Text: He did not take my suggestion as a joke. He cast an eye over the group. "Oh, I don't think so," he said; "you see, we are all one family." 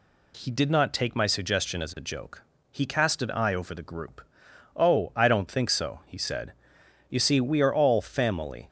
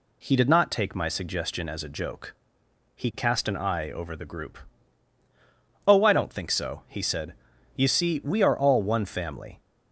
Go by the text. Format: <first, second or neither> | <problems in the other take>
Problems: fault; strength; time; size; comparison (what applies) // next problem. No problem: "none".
second | skips "one"; at 7.9 s